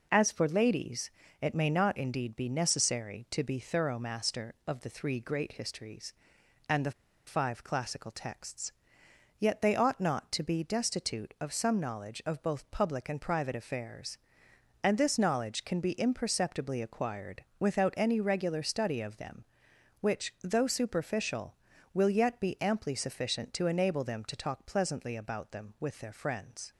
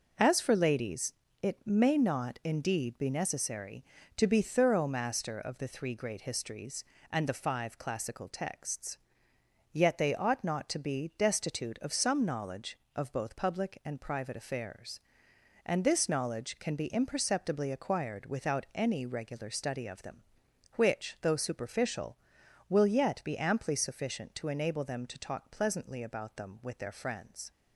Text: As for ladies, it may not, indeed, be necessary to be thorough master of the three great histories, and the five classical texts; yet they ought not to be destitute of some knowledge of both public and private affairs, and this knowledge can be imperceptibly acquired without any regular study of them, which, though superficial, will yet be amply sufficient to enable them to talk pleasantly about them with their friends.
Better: second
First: pauses between "the" and "five"; slight; at 6.9 s; 0.34 s long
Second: none

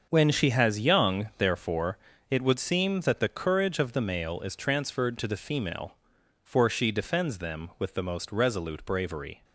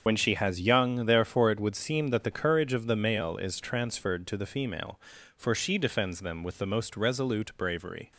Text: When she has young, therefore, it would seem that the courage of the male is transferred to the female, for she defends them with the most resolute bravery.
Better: first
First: starts louder than the rest; until 1.1 s; 6.5 dB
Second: loses the start of "When"; at 0.0 s; 70 ms // starts louder than the rest; until 1.0 s; 6.5 dB

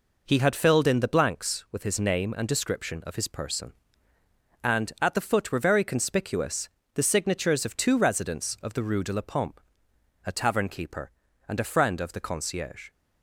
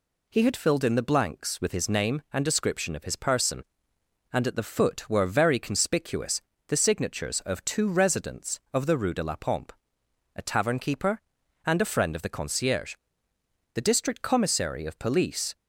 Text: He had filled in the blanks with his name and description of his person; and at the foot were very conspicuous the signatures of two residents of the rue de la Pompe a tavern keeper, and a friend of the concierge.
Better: first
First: pauses between "conspicuous" and "the"; slight; at 6.6 s; 0.26 s long // pauses between "Pompe" and "a"; noticeable; at 9.6 s; 0.62 s long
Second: pauses between "conspicuous" and "the"; slight; at 6.4 s; 0.26 s long // pauses between "Pompe" and "a"; noticeable; at 9.7 s; 0.62 s long // goes on to say "The district Commissary of Police"; strong; from 13.7 s on; 1.8 s long

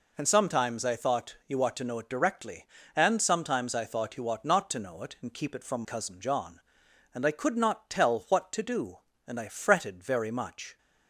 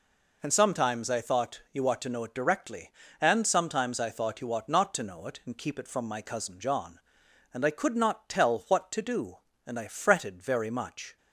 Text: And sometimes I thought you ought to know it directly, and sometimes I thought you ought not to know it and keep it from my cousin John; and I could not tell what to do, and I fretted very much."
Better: second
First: skips "my"; at 5.8 s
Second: none

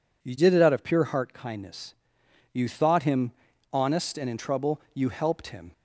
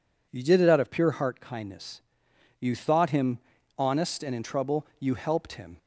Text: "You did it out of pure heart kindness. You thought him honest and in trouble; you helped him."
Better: neither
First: pauses between "him" and "honest"; at 3.3 s; 0.42 s long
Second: pauses between "him" and "honest"; at 3.3 s; 0.40 s long

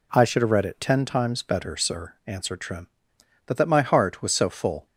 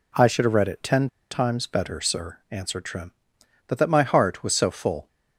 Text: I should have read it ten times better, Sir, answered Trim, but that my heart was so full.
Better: first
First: none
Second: pauses between "ten" and "times"; slight; at 1.0 s; 0.23 s long

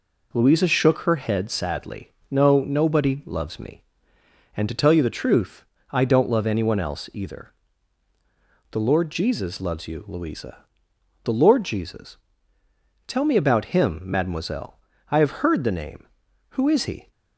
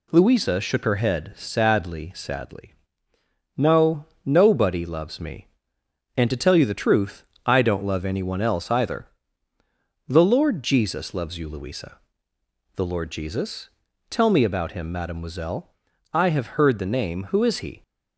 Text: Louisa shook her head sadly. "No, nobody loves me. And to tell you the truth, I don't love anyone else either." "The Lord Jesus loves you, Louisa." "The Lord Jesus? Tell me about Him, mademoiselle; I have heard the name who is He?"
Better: first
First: none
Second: says "sadly" twice; at 2.1 s

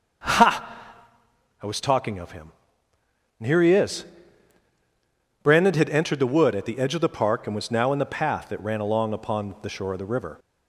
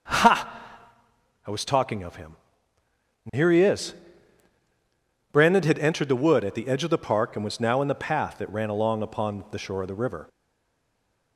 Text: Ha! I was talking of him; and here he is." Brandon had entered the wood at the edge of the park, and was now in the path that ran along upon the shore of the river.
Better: first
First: starts louder than the rest; until 2.0 s; 6.5 dB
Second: starts louder than the rest; until 1.9 s; 6.5 dB // stays silent after the last word; from 10.2 s on; 1.1 s long

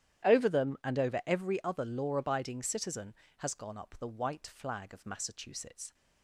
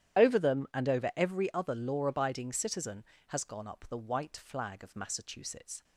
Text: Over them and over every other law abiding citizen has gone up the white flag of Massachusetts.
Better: first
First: starts louder than the rest; strong; until 1.3 s; 11 dB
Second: loses the start of "Over"; at 0.1 s; 40 ms // starts louder than the rest; strong; until 1.2 s; 11 dB

